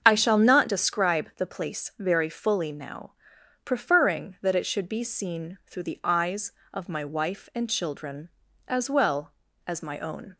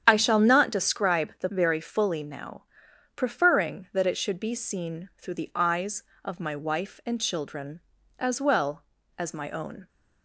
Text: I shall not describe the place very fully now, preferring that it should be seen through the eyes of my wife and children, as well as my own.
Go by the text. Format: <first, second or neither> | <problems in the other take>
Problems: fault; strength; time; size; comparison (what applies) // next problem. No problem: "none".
first | starts louder than the rest; strong; until 1.0 s; 9 dB; strong in the first // skips "place"; at 1.4 s